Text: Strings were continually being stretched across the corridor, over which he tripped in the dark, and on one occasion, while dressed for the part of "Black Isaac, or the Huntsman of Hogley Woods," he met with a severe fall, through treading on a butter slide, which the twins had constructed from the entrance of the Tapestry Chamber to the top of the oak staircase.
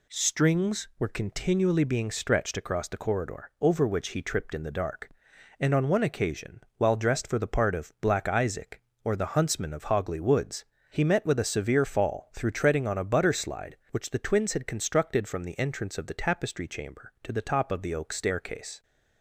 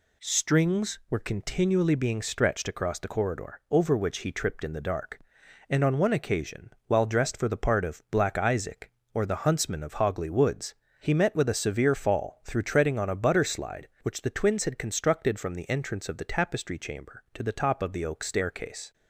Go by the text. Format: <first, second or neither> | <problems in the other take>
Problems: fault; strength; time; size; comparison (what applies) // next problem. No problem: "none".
neither | none